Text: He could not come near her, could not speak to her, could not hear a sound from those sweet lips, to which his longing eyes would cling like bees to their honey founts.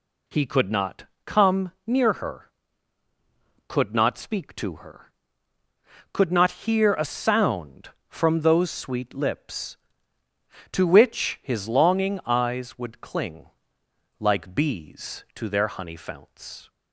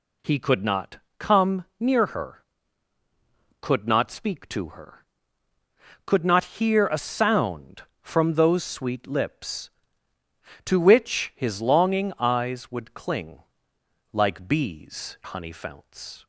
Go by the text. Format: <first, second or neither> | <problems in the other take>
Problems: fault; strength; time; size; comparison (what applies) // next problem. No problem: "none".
first | pauses between "not" and "come"; slight; at 0.9 s; 0.20 s long; slight in the first // pauses between "cling" and "like"; noticeable; at 13.4 s; 0.70 s long; noticeable in the first // skips "to their"; at 15.2 s